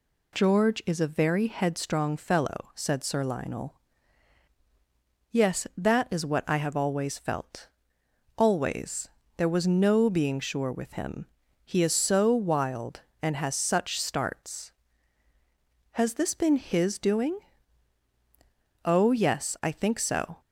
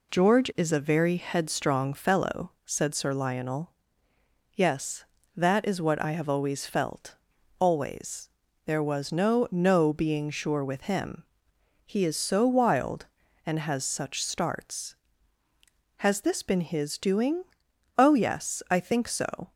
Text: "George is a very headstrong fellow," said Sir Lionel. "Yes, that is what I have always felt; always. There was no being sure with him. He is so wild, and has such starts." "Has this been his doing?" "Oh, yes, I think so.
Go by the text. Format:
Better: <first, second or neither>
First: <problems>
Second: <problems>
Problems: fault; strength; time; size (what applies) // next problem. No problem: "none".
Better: first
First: none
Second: says "no" twice; at 9.5 s